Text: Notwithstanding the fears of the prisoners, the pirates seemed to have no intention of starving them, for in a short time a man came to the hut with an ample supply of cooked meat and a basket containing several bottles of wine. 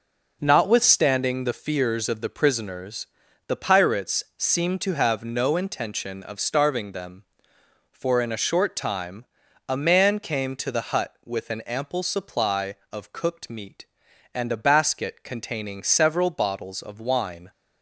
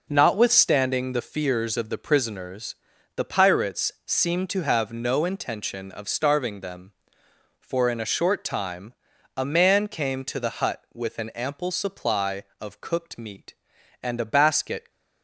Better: first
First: pauses between "time" and "a"; at 9.2 s; 0.42 s long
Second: pauses between "time" and "a"; at 8.9 s; 0.42 s long // stops before "containing several bottles of wine"; at 14.9 s

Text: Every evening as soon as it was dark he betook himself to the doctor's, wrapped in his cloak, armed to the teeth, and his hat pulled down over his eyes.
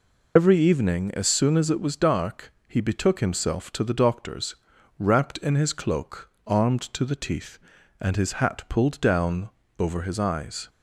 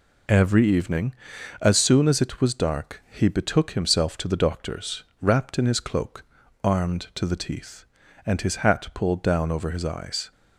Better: second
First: loses the start of "Every"; at 0.3 s; 85 ms // pauses between "dark" and "he"; slight; at 2.5 s; 0.16 s long // pauses between "down" and "over"; slight; at 9.5 s; 0.28 s long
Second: none

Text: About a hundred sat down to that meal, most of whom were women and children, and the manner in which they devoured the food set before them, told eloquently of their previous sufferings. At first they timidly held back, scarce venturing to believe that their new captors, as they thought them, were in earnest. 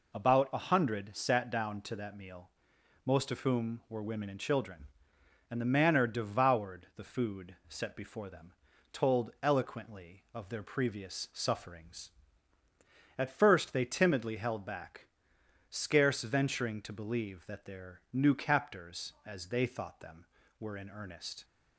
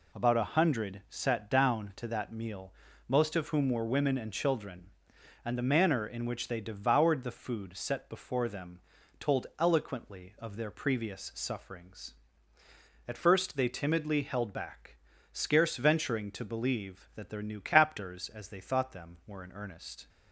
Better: second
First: skips "in which they"; at 6.0 s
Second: none

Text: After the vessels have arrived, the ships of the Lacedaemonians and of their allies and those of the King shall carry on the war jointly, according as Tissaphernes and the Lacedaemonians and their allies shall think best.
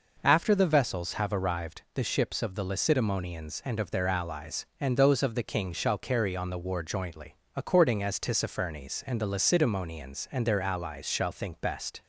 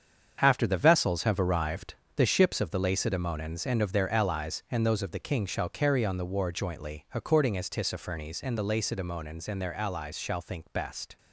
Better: first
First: none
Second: gets quieter; strong; throughout; 9 dB

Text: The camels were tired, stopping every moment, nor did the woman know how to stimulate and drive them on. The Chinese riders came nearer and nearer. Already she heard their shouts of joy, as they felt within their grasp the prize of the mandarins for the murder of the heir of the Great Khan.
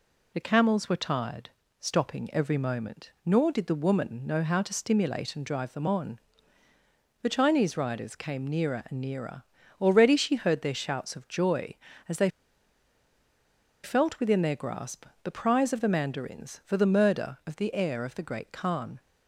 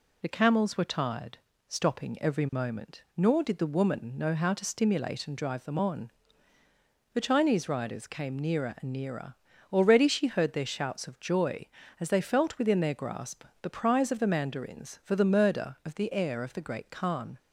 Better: second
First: pauses between "they" and "felt"; strong; at 12.2 s; 1.5 s long // pauses between "grasp" and "the"; slight; at 15.0 s; 0.18 s long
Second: pauses between "grasp" and "the"; slight; at 13.4 s; 0.18 s long

